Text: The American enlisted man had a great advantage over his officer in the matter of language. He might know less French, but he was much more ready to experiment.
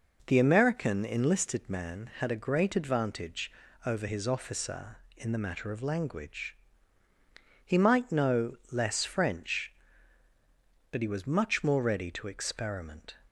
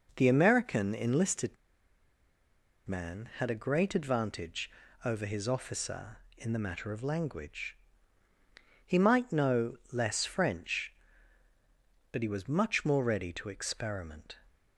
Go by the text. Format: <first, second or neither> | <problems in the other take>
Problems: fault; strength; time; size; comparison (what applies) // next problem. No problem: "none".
first | pauses between "enlisted" and "man"; strong; at 1.5 s; 1.3 s long // pauses between "advantage" and "over"; slight; at 4.6 s; 0.34 s long; slight in the first